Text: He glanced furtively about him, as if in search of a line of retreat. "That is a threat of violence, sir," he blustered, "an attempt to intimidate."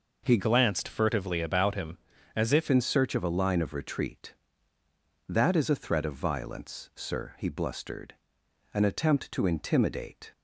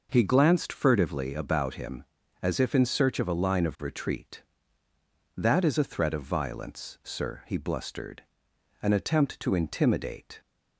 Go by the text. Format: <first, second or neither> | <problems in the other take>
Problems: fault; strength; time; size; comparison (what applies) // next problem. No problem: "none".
second | changes voice from "glanced" to "if"; from 0.3 to 2.6 s; 2.3 s long